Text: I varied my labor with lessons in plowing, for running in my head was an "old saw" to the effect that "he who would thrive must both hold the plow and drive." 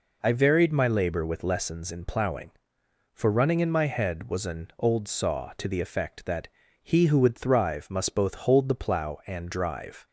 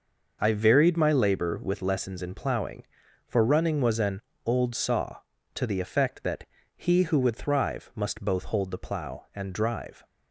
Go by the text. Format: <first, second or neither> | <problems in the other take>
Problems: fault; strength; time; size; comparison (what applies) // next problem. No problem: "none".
first | skips "in my head"; at 3.8 s // pauses between "an" and "old"; slight; at 4.2 s; 0.24 s long // pauses between "that" and "he"; slight; at 6.4 s; 0.32 s long; slight in the first